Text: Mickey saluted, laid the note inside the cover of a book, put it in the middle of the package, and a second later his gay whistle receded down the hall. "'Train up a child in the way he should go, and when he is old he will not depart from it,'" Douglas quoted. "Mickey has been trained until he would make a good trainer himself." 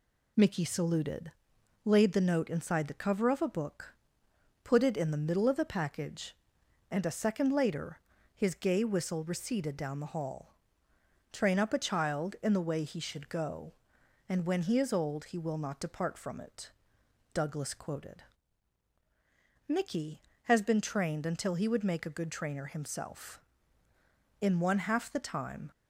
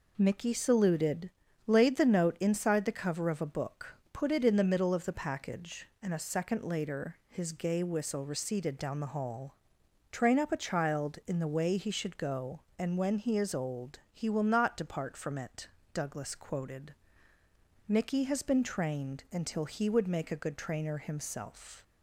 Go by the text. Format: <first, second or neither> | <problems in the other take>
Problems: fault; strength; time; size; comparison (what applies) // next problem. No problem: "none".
second | pauses between "later" and "his"; slight; at 8.0 s; 0.34 s long // goes on to say "In one half the time"; noticeable; from 24.4 s on; 1.3 s long